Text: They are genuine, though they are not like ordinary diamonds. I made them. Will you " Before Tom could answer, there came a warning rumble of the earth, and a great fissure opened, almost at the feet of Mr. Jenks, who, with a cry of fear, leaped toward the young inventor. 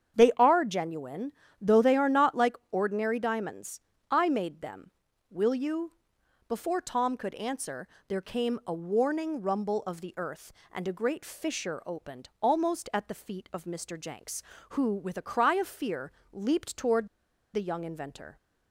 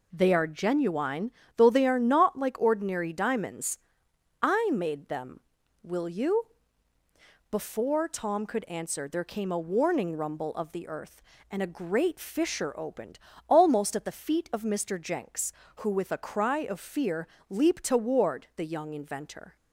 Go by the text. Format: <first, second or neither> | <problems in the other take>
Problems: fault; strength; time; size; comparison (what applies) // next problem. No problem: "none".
second | starts louder than the rest; strong; until 1.2 s; 8 dB // pauses between "toward" and "the"; noticeable; at 17.0 s; 0.46 s long